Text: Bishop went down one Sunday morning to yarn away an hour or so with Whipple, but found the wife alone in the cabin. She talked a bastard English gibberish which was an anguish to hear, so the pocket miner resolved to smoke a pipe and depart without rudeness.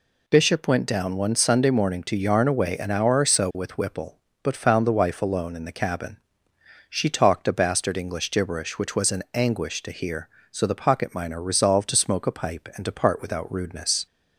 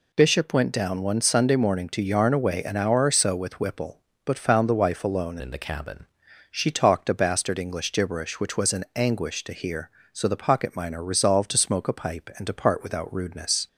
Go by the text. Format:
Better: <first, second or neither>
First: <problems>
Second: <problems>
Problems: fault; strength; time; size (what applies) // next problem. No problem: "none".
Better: first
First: none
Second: changes voice from "in" to "cabin"; from 5.4 to 6.0 s; 0.6 s long